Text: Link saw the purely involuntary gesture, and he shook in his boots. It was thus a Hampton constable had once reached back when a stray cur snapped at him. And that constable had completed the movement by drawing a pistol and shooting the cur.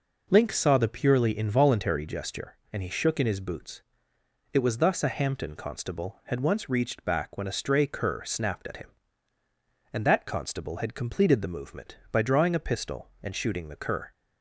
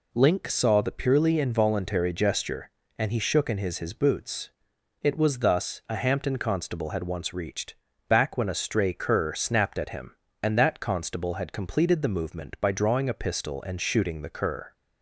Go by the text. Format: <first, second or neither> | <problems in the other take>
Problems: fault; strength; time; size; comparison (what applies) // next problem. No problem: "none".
first | says "his" twice; at 3.7 s // pauses between "reached" and "back"; slight; at 7.7 s; 0.34 s long